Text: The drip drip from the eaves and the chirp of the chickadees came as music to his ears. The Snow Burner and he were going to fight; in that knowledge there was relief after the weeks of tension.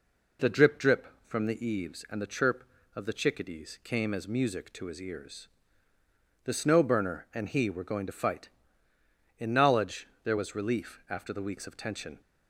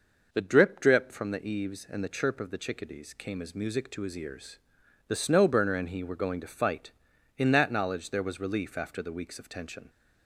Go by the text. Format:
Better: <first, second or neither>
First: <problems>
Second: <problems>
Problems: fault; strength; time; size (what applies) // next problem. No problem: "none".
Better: second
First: skips "that"; at 9.5 s // pauses between "knowledge" and "there"; slight; at 10.0 s; 0.18 s long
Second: none